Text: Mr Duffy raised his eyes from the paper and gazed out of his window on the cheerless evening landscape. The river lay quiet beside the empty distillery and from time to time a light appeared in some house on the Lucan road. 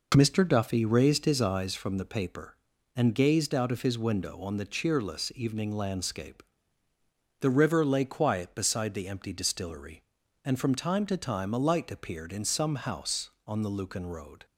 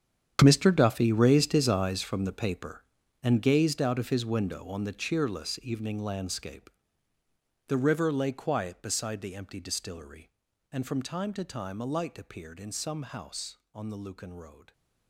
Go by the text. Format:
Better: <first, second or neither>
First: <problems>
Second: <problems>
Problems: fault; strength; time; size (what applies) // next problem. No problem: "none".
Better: first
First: none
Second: gets quieter; strong; throughout; 15 dB